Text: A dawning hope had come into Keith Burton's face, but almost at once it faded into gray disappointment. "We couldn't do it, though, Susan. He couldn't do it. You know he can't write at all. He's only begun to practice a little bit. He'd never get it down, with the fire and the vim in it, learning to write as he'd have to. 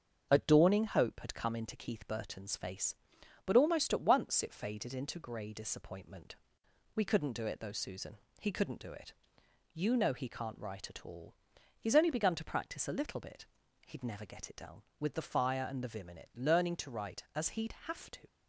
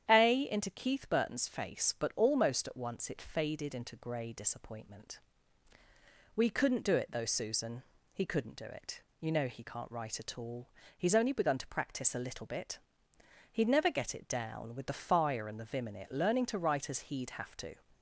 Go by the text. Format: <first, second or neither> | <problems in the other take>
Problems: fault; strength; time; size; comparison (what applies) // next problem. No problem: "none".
first | starts louder than the rest; strong; until 1.1 s; 9.5 dB; also in the first // skips "dawning hope had come"; at 0.4 s